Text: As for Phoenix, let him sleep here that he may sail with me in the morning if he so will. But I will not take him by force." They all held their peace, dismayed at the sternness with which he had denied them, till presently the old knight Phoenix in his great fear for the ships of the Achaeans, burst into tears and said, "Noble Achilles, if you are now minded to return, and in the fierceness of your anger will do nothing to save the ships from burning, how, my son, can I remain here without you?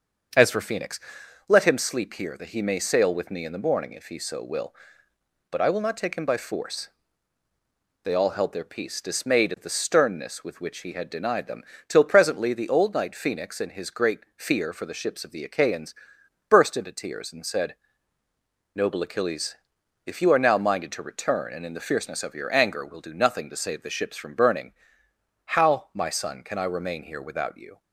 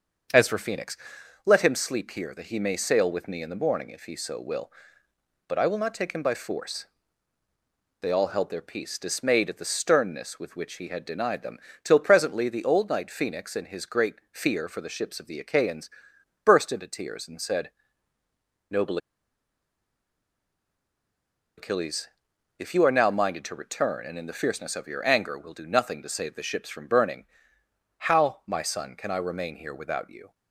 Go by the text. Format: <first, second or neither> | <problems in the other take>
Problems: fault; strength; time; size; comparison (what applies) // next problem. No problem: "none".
first | starts louder than the rest; until 1.8 s; 6.5 dB; also in the first // pauses between "great" and "fear"; slight; at 14.1 s; 0.16 s long; slight in the first // pauses between "Noble" and "Achilles"; strong; at 18.9 s; 2.6 s long